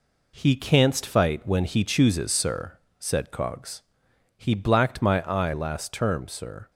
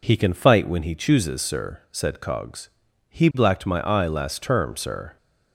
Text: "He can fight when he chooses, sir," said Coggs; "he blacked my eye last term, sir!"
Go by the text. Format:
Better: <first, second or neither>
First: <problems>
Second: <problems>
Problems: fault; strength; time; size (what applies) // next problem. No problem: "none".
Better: second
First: says "canst" for "can"; at 0.5 s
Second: none